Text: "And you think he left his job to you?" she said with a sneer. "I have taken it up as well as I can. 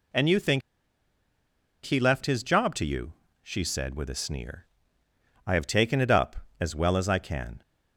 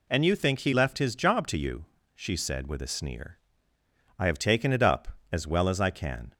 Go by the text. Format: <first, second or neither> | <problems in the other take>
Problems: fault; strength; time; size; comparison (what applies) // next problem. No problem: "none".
second | pauses between "think" and "he"; at 0.6 s; 1.2 s long